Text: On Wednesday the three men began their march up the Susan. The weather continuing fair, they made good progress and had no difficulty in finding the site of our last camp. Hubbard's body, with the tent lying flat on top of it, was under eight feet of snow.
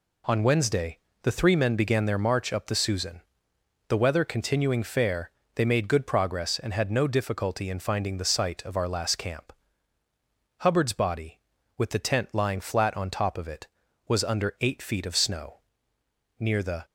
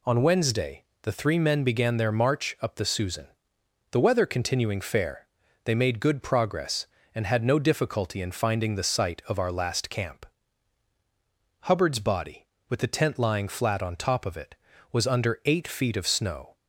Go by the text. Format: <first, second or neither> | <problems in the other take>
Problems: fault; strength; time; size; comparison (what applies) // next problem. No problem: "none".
second | pauses between "Wednesday" and "the"; slight; at 0.9 s; 0.22 s long; slight in the second // goes on to say "Near the"; slight; from 16.3 s on; 0.46 s long